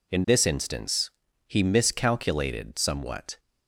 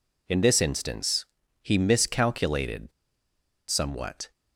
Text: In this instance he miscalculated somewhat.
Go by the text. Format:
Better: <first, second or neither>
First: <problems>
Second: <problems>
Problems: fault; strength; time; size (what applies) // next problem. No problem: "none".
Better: first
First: pauses between "instance" and "he"; slight; at 1.1 s; 0.36 s long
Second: pauses between "instance" and "he"; slight; at 1.2 s; 0.36 s long // pauses between "miscalculated" and "somewhat"; noticeable; at 2.9 s; 0.79 s long